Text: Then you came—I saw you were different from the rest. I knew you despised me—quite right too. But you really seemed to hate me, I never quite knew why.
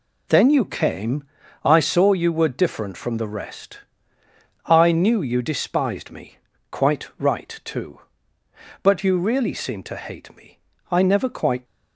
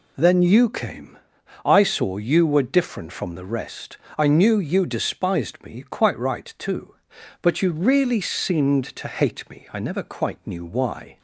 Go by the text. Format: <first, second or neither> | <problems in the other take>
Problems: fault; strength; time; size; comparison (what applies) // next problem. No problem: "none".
second | stops before "knew why"; at 11.6 s